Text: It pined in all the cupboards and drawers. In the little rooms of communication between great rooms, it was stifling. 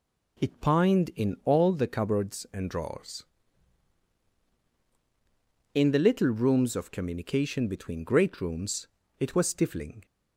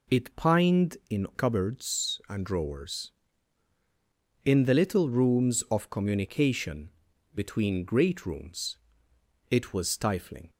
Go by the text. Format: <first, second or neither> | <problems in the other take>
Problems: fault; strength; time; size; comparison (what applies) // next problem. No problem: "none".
first | skips "all the"; at 1.3 s // pauses between "communication" and "between"; at 6.9 s; 0.44 s long